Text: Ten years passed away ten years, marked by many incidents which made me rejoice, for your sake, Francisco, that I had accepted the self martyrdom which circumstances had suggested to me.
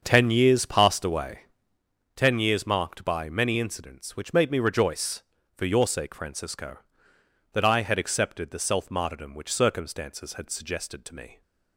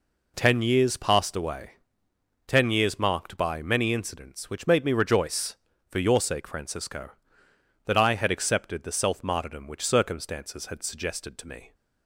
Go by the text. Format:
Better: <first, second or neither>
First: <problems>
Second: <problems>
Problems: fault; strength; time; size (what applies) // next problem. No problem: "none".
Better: second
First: starts louder than the rest; until 1.9 s; 6.5 dB // pauses between "away" and "ten"; noticeable; at 1.3 s; 0.76 s long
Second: pauses between "away" and "ten"; noticeable; at 1.7 s; 0.76 s long